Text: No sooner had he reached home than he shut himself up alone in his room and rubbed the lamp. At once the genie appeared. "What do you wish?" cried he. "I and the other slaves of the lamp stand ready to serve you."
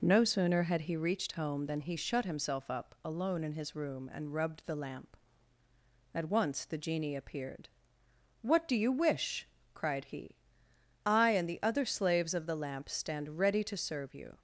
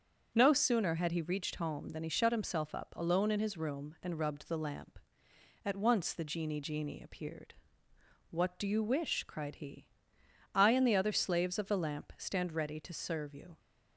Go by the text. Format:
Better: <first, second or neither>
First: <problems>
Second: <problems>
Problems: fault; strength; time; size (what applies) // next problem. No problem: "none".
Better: first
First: none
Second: starts louder than the rest; until 1.3 s; 7 dB // says "genie" twice; at 6.6 s